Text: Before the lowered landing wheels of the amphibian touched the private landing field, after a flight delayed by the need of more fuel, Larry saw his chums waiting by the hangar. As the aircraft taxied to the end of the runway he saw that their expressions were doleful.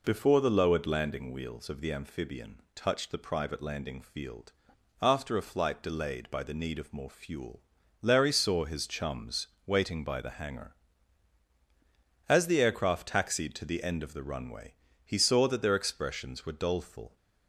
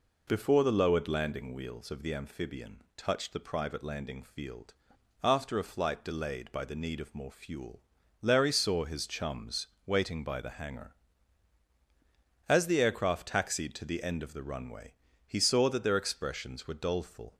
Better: neither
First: pauses between "chums" and "waiting"; slight; at 9.4 s; 0.18 s long // pauses between "runway" and "he"; slight; at 14.7 s; 0.30 s long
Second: pauses between "chums" and "waiting"; slight; at 9.6 s; 0.18 s long // pauses between "runway" and "he"; slight; at 14.9 s; 0.32 s long

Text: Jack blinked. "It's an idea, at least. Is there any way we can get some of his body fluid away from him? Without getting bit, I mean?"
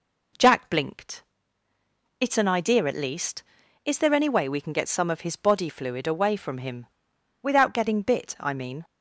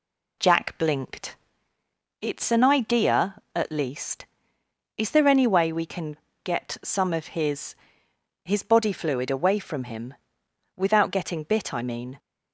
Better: first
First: none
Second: pauses between "can" and "get"; slight; at 6.1 s; 0.26 s long // says "his" twice; at 8.4 s

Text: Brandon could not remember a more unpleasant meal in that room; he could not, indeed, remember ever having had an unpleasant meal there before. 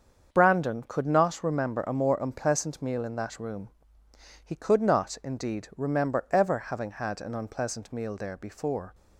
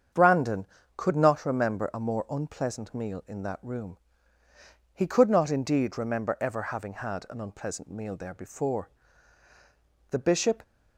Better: first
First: starts louder than the rest; until 1.3 s; 7 dB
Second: starts louder than the rest; strong; until 1.4 s; 7.5 dB // goes on to say "The Bishop"; from 10.1 s on; 0.52 s long

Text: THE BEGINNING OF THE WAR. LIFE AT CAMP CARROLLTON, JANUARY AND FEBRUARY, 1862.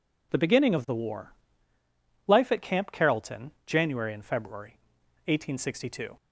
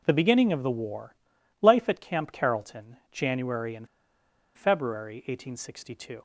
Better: first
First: none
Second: pauses between "AND" and "FEBRUARY"; noticeable; at 3.8 s; 0.68 s long

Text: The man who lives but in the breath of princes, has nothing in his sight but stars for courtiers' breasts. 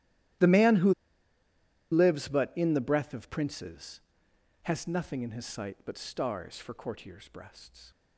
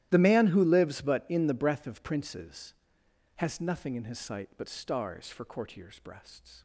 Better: second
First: starts louder than the rest; strong; until 2.4 s; 14 dB // pauses between "who" and "lives"; at 0.9 s; 0.98 s long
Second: starts louder than the rest; strong; until 1.1 s; 14 dB

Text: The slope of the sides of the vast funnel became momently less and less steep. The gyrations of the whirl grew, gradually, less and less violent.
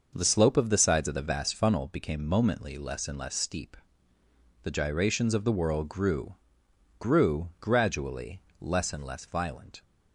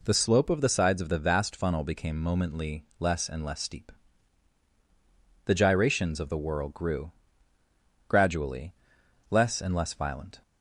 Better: second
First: starts louder than the rest; noticeable; until 1.1 s; 6 dB // says "grew" twice; at 6.9 s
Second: none

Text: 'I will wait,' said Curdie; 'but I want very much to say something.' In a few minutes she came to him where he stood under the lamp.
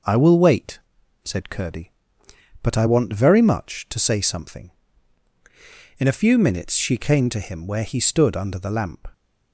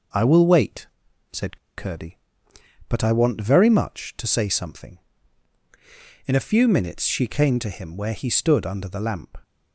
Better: first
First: none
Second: pauses between "said" and "Curdie"; slight; at 1.5 s; 0.20 s long

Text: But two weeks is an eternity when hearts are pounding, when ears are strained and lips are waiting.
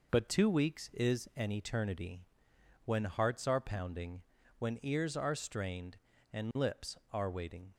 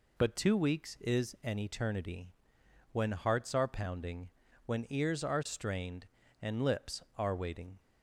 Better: second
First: gets quieter; noticeable; throughout; 4.5 dB // pauses between "eternity" and "when"; noticeable; at 2.2 s; 0.62 s long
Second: pauses between "eternity" and "when"; noticeable; at 2.2 s; 0.62 s long

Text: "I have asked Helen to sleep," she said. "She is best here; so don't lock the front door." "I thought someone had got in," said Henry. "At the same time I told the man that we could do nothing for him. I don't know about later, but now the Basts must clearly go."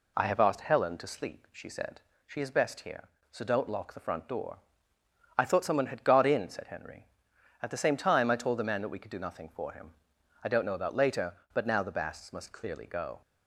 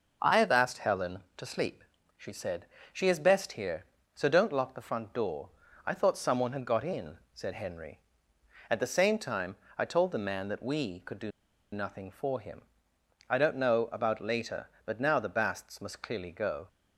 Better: first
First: none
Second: pauses between "time" and "I"; slight; at 9.5 s; 0.20 s long // pauses between "do" and "nothing"; at 11.2 s; 0.43 s long

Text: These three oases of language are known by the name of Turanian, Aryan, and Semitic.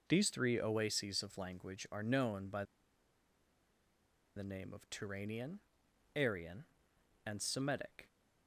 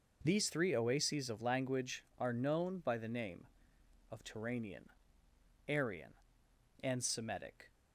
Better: second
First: pauses between "by" and "the"; strong; at 2.6 s; 1.7 s long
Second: none

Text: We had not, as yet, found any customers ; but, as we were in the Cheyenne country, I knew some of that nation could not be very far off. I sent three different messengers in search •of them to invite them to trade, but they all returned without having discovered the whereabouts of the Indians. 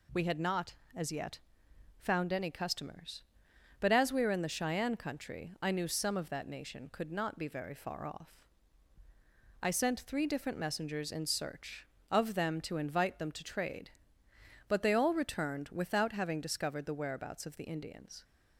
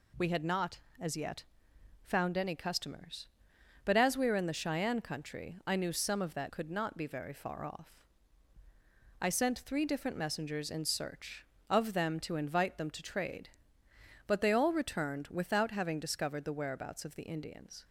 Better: first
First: none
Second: skips "nation"; at 6.4 s

